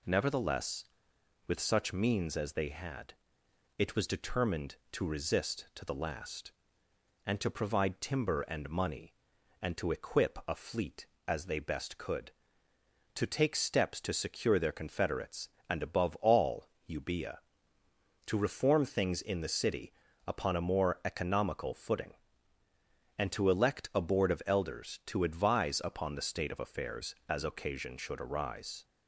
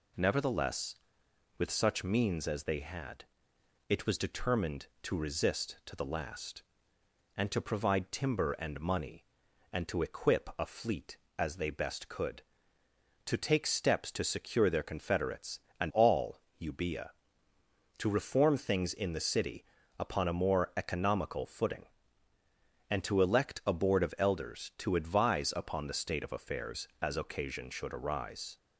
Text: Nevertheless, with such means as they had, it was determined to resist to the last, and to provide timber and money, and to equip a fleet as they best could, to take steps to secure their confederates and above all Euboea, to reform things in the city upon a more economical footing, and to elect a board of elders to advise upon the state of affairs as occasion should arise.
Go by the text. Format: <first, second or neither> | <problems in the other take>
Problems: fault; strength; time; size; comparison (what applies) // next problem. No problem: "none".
first | skips "above"; at 15.9 s // pauses between "all" and "Euboea"; slight; at 16.3 s; 0.22 s long; slight in the first // pauses between "city" and "upon"; slight; at 19.6 s; 0.34 s long; slight in the first